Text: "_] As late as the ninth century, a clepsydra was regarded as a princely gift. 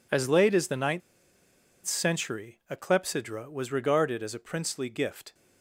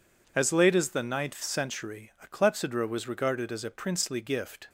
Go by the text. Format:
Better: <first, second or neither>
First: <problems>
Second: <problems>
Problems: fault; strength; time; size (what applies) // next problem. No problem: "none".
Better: second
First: pauses between "ninth" and "century"; noticeable; at 1.0 s; 0.85 s long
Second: none